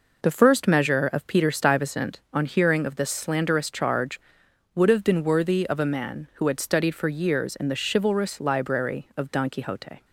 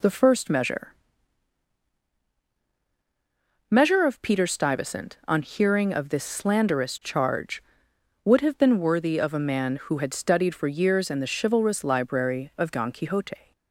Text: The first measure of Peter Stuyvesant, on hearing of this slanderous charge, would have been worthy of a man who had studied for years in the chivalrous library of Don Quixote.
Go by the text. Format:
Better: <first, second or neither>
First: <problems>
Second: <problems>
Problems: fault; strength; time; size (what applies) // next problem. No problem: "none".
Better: first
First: none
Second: says "measure" twice; at 3.6 s